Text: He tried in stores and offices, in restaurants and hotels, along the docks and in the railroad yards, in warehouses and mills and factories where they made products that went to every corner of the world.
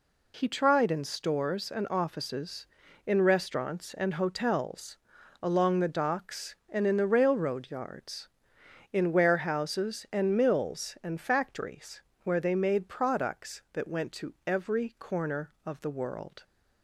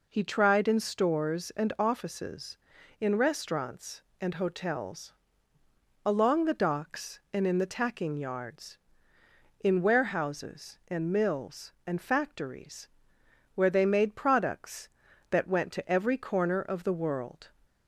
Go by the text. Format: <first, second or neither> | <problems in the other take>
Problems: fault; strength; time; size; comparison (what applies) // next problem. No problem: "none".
first | says "tacking" for "railroad"; at 7.6 s // pauses between "factories" and "where"; noticeable; at 12.8 s; 0.66 s long; slight in the first